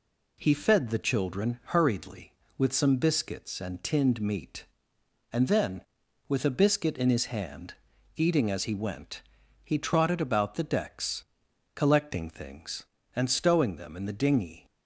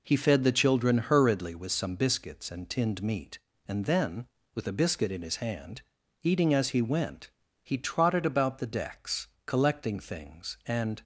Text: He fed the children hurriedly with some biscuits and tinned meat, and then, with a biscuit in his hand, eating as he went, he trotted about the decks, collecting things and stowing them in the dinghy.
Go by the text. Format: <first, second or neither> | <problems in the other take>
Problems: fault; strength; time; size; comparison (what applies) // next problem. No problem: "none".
first | stops before "stowing them in the dinghy"; at 11.0 s